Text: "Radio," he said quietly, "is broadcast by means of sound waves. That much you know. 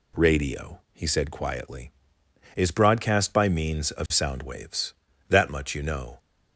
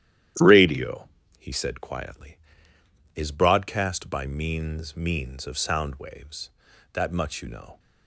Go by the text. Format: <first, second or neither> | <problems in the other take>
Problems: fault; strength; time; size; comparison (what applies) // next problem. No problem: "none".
first | starts louder than the rest; strong; until 1.6 s; 11.5 dB // says "means" twice; at 4.9 s